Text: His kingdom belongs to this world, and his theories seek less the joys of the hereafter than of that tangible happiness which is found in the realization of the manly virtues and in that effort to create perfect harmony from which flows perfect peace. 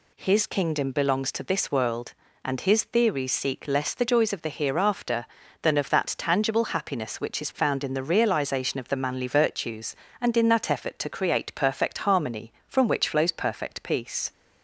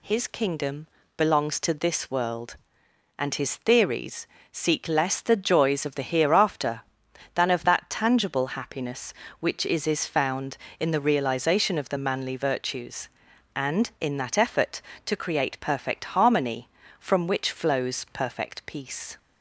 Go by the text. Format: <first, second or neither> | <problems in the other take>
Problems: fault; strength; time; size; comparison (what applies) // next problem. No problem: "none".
first | pauses between "kingdom" and "belongs"; slight; at 0.8 s; 0.28 s long // pauses between "theories" and "seek"; slight; at 4.2 s; 0.24 s long // says "is" twice; at 9.8 s